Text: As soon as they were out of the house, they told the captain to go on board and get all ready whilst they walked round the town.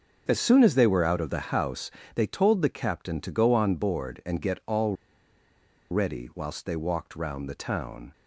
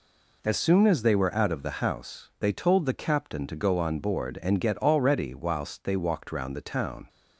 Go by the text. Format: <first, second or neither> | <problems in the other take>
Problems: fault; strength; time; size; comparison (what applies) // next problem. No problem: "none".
second | starts louder than the rest; until 1.2 s; 7 dB // pauses between "all" and "ready"; noticeable; at 4.9 s; 0.97 s long